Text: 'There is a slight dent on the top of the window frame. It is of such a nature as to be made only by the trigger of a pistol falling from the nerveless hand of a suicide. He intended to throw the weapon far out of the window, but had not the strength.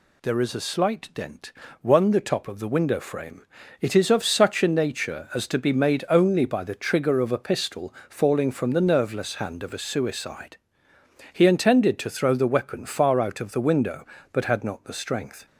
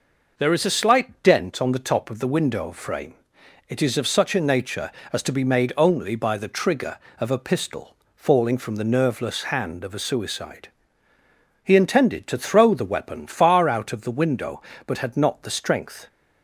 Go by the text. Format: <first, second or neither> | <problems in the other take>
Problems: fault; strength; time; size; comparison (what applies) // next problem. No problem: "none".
second | says "one" for "on"; at 1.8 s // pauses between "pistol" and "falling"; slight; at 7.9 s; 0.16 s long; slight in the second